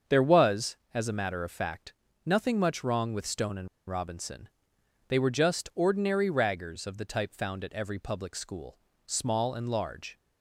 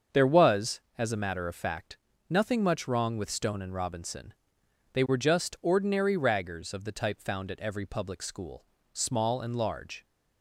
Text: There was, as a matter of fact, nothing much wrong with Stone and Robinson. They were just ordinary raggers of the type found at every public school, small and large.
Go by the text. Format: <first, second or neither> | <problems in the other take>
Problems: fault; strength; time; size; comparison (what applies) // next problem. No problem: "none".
second | starts louder than the rest; until 1.2 s; 7 dB; also in the second // pauses between "and" and "Robinson"; slight; at 3.6 s; 0.19 s long